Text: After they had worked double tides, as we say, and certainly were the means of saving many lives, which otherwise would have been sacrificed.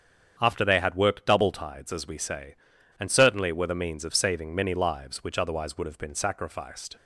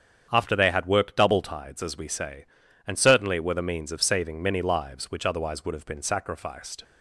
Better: neither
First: starts louder than the rest; strong; until 1.3 s; 8 dB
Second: starts louder than the rest; strong; until 1.3 s; 8 dB

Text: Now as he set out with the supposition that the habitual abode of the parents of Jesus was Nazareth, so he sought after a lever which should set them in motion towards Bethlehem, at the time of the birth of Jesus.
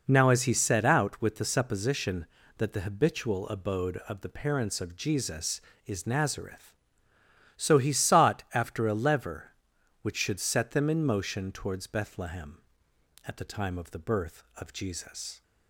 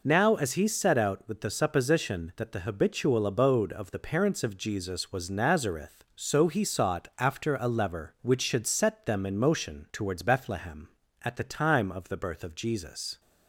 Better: second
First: says "is" for "was"; at 5.8 s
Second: none

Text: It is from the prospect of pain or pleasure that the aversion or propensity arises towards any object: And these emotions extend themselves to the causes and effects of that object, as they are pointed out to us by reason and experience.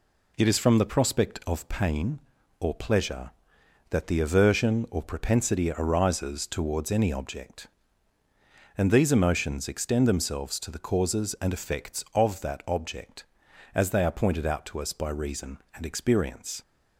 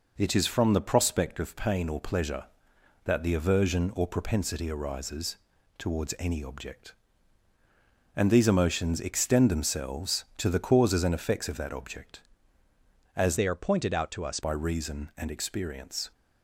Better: first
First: none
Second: pauses between "arises" and "towards"; at 5.3 s; 0.40 s long // changes voice from "they" to "us"; from 13.3 to 14.3 s; 1.0 s long

